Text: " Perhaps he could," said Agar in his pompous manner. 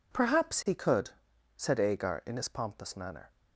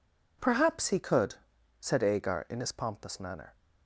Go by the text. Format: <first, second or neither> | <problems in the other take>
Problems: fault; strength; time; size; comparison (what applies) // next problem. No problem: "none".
neither | none